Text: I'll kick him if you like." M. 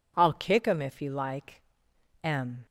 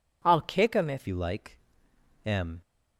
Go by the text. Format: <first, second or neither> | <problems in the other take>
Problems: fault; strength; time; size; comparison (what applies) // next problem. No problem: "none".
first | changes voice at "you"; from 1.0 s on; 1.6 s long